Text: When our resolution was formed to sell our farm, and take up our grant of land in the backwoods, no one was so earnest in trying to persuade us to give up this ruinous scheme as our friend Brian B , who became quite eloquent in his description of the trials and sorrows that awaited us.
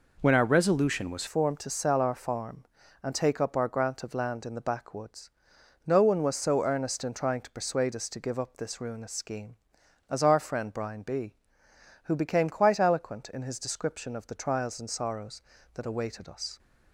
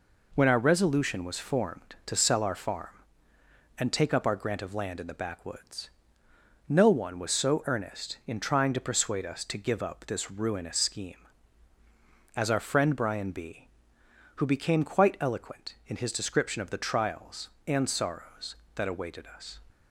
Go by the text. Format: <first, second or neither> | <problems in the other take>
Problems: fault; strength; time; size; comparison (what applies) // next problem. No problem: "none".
second | changes voice at "formed"; from 1.2 s on; 15.3 s long